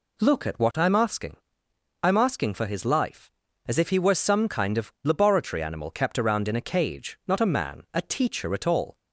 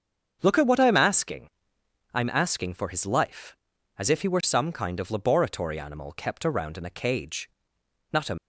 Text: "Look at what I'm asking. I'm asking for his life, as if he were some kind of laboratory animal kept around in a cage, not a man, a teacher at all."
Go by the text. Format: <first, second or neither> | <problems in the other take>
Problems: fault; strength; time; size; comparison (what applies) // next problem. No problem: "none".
first | starts louder than the rest; until 1.4 s; 7 dB // stops before "man a teacher at all"; at 8.3 s